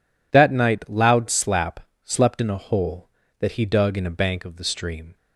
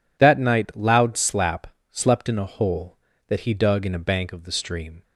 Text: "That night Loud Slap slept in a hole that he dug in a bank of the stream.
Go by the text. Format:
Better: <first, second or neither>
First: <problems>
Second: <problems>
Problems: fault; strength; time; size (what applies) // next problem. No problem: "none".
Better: neither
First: pauses between "Slap" and "slept"; slight; at 1.8 s; 0.22 s long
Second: pauses between "Slap" and "slept"; slight; at 1.6 s; 0.22 s long